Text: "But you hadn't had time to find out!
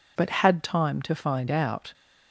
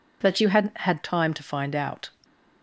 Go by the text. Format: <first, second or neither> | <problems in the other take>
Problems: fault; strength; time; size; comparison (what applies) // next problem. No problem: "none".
second | skips "you hadn't"; at 0.2 s